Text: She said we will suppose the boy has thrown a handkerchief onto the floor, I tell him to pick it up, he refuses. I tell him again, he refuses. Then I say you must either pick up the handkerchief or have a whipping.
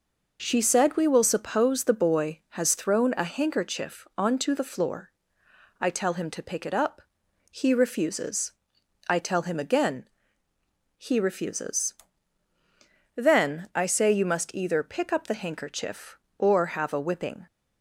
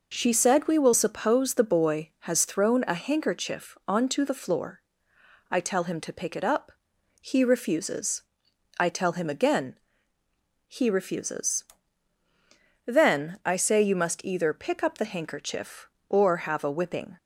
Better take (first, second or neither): neither